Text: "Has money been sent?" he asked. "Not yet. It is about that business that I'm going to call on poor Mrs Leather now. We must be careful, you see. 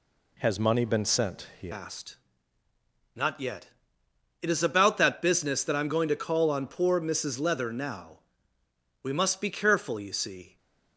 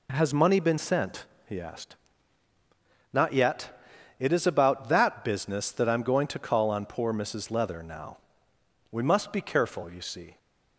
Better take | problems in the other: second | changes voice at "asked"; from 1.7 s on; 8.8 s long

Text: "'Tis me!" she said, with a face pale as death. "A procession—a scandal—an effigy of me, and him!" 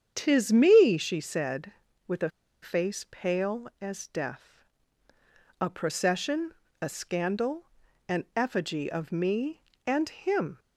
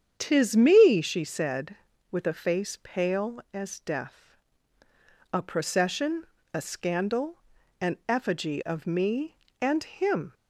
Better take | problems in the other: second | starts louder than the rest; strong; until 1.1 s; 8 dB; strong in the second // pauses between "a" and "face"; slight; at 2.2 s; 0.32 s long

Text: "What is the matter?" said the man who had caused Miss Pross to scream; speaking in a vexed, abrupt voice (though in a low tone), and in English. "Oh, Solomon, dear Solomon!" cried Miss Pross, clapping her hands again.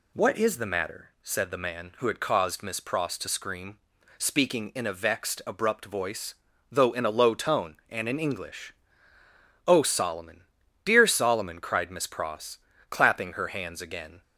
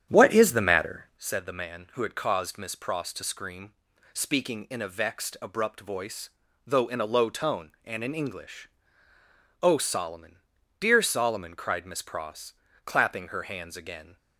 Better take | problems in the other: first | starts louder than the rest; strong; until 1.2 s; 9.5 dB

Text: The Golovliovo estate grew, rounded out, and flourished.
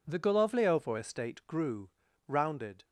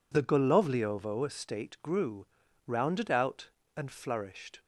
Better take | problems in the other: second | stops before "out and flourished"; at 2.8 s

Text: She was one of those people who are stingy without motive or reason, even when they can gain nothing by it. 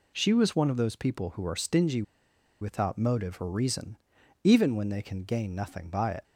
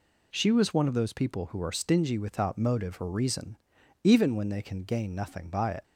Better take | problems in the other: second | pauses between "stingy" and "without"; noticeable; at 2.0 s; 0.58 s long

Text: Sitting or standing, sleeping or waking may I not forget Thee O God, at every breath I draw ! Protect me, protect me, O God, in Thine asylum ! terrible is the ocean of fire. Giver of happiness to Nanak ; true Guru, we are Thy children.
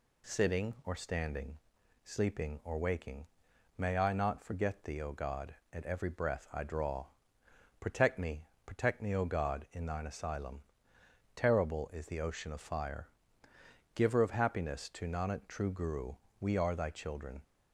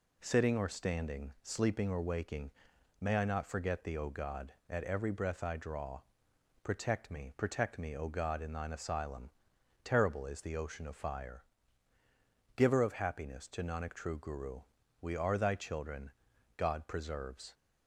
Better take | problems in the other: first | pauses between "waking" and "may"; noticeable; at 2.5 s; 0.48 s long; noticeable in the first // goes on to say "God preserves"; noticeable; from 16.5 s on; 0.96 s long

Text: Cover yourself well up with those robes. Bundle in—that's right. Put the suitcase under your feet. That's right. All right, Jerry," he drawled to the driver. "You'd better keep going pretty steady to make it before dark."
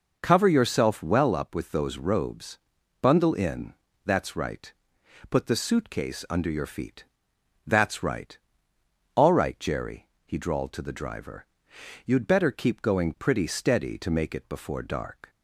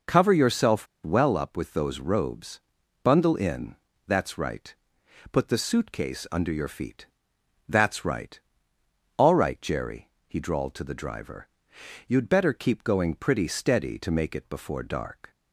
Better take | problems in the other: first | pauses between "yourself" and "well"; slight; at 0.8 s; 0.17 s long

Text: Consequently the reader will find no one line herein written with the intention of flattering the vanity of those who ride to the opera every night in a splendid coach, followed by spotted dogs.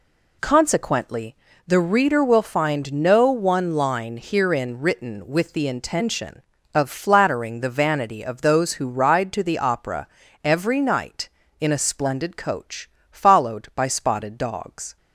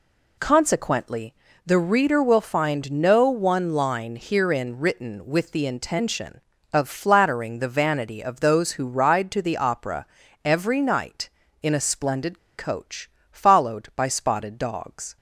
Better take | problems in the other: first | pauses between "Consequently" and "the"; slight; at 1.3 s; 0.32 s long; slight in the first // pauses between "opera" and "every"; at 10.0 s; 0.38 s long; also in the first // pauses between "splendid" and "coach"; slight; at 12.3 s; 0.19 s long

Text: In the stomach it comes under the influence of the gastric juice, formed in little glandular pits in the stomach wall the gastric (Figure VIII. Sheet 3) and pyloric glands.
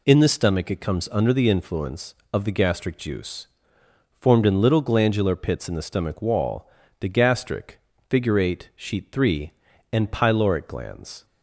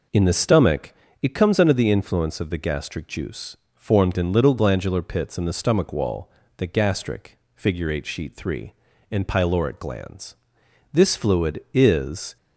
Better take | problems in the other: first | pauses between "stomach" and "it"; slight; at 0.9 s; 0.26 s long // pauses between "wall" and "the"; slight; at 6.3 s; 0.26 s long; slight in the first // goes on to say "This fluid is"; from 10.9 s on; 1.4 s long

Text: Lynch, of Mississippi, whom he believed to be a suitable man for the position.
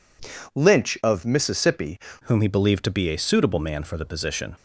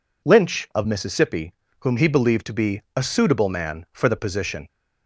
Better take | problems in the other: second | changes voice at "whom"; from 2.2 s on; 2.3 s long

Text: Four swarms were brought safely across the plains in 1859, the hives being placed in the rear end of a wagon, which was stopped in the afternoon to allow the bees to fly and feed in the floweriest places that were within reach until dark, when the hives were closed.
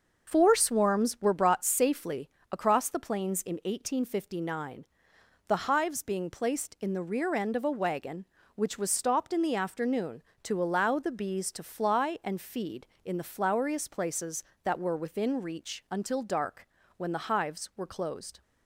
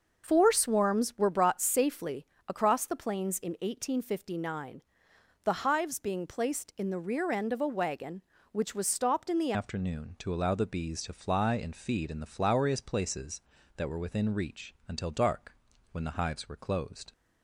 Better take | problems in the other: first | starts louder than the rest; until 1.3 s; 6 dB; also in the first // pauses between "safely" and "across"; slight; at 2.2 s; 0.24 s long; slight in the first // changes voice at "afternoon"; from 9.5 s on; 7.6 s long

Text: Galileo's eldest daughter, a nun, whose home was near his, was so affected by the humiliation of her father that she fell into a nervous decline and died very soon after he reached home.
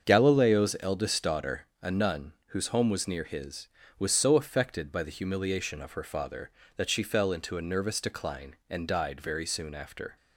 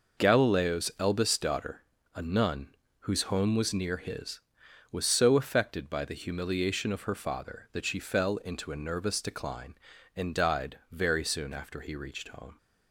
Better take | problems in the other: second | starts louder than the rest; until 1.1 s; 7 dB // stops before "he reached home"; at 10.1 s

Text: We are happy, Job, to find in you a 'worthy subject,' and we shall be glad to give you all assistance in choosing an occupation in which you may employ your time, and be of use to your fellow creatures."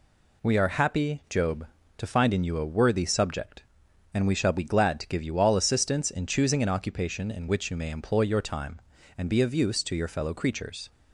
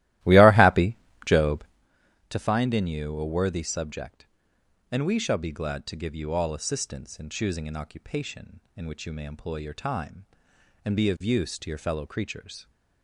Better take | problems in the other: first | starts louder than the rest; strong; until 1.9 s; 15.5 dB

